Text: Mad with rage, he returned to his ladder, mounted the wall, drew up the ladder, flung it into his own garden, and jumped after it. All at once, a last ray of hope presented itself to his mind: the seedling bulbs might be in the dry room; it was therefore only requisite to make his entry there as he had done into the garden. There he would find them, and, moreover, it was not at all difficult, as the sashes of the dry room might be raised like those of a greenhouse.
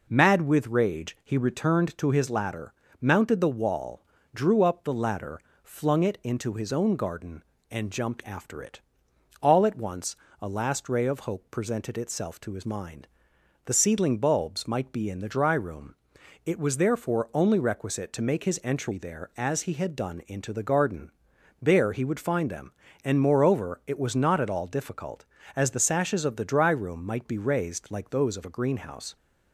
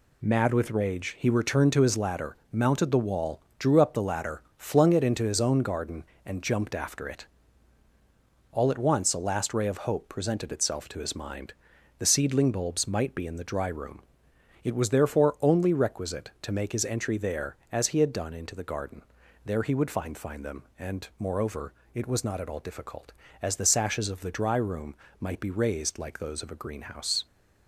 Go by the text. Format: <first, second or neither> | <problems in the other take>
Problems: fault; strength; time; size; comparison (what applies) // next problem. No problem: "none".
first | says "find" twice; at 20.1 s // pauses between "room" and "might"; slight; at 24.9 s; 0.26 s long